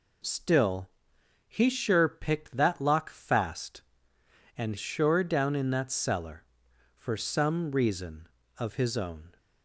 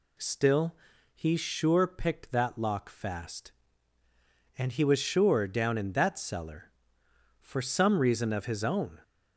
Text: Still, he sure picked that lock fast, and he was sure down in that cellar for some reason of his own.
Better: second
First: skips "he was"; at 4.7 s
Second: none

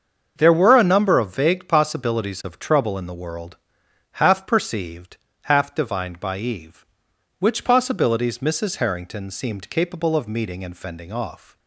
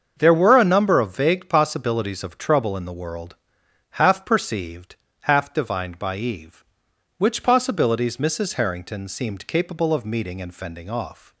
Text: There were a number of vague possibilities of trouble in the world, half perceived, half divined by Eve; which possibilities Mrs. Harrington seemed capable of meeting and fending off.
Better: neither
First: starts louder than the rest; until 1.3 s; 6.5 dB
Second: starts louder than the rest; until 1.1 s; 6.5 dB

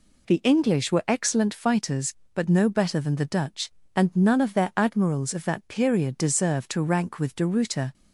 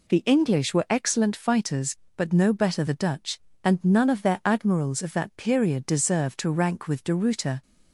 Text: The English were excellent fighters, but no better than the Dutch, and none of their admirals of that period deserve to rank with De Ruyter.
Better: first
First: none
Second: skips "than"; at 2.8 s

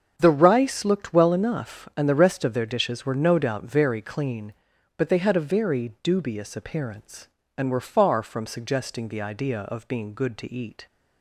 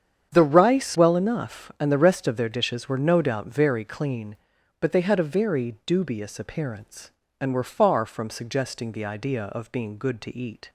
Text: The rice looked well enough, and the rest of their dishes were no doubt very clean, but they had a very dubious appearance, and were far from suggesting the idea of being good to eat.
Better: first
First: starts louder than the rest; until 1.1 s; 7 dB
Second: starts louder than the rest; strong; until 1.3 s; 8 dB // skips "looked"; at 0.9 s

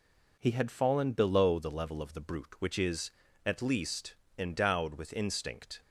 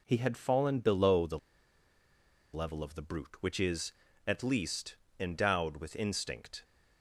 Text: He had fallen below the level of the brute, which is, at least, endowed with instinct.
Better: first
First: none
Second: pauses between "the" and "level"; at 1.3 s; 1.1 s long

